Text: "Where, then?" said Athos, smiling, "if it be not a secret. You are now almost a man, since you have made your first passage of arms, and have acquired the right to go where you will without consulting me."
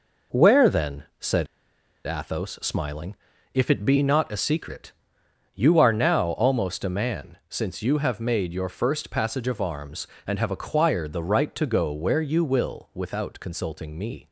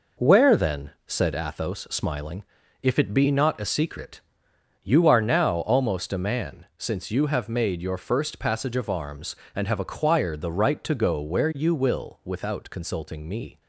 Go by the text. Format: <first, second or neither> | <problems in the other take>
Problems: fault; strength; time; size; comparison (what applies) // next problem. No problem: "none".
second | pauses between "said" and "Athos"; noticeable; at 1.4 s; 0.61 s long